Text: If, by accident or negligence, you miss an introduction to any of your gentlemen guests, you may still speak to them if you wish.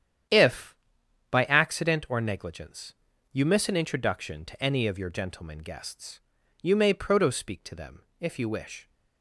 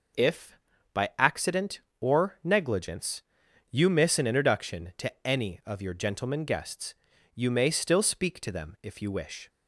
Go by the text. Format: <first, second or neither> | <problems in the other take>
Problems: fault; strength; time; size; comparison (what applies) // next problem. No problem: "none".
second | starts louder than the rest; strong; until 1.8 s; 9.5 dB // says "proto" for "still"; at 6.9 s // pauses between "them" and "if"; slight; at 8.0 s; 0.18 s long